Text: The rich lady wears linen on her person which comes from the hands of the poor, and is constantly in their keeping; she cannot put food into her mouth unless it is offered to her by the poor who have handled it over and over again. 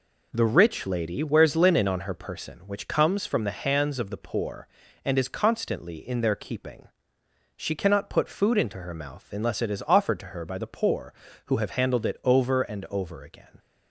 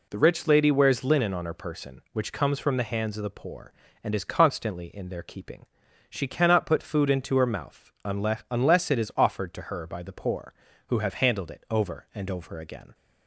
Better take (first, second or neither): first